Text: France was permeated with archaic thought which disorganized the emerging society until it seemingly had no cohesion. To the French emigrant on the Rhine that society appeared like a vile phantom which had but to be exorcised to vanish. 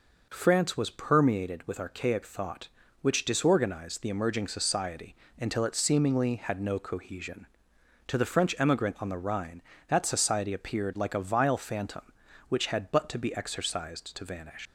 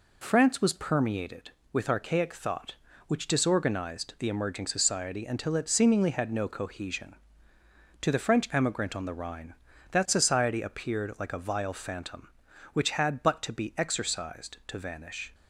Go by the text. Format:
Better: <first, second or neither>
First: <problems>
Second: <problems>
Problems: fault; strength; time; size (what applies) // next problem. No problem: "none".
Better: second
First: pauses between "society" and "until"; slight; at 5.1 s; 0.24 s long // leaves "vanish" unfinished; at 14.6 s; 110 ms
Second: none